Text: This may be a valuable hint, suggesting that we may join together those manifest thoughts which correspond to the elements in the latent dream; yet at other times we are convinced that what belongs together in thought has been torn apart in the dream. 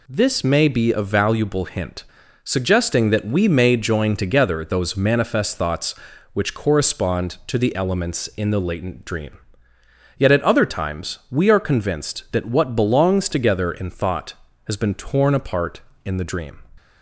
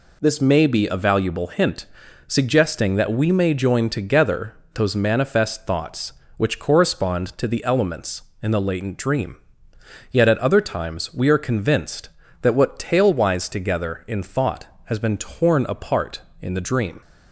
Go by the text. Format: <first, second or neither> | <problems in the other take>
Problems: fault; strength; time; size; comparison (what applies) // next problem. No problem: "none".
first | pauses between "together" and "those"; slight; at 4.5 s; 0.20 s long // says "tailwise" for "belongs"; at 12.7 s